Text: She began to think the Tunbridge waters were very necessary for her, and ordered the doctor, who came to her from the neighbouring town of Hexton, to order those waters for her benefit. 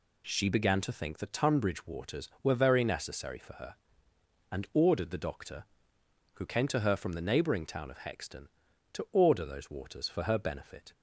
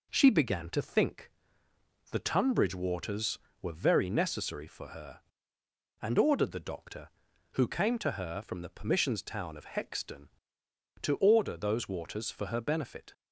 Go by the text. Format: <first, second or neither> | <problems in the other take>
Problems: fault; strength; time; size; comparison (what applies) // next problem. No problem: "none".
first | pauses between "think" and "the"; noticeable; at 1.2 s; 0.82 s long // says "permissions" for "neighbouring"; at 8.6 s